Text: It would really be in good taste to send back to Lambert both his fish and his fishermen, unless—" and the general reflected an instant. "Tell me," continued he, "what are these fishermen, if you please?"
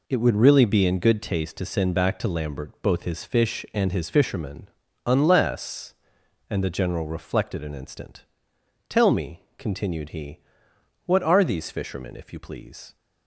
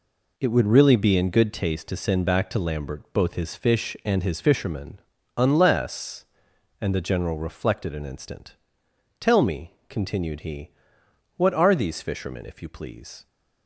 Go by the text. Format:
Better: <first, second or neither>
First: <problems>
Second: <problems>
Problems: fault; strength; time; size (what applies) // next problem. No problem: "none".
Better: neither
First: none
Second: none